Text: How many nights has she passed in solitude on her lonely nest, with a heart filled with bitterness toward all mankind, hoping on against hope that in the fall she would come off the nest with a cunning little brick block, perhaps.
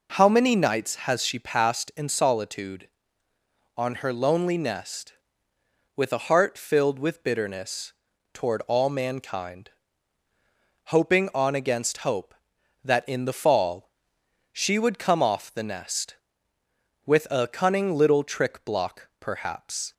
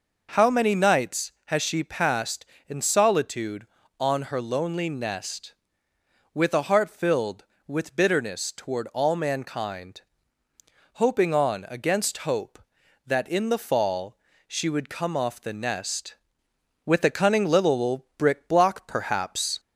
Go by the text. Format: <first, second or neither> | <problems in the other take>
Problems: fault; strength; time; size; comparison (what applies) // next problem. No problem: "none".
second | pauses between "bitterness" and "toward"; at 7.9 s; 0.40 s long // pauses between "fall" and "she"; noticeable; at 13.8 s; 0.62 s long; slight in the second // says "trick" for "brick"; at 18.2 s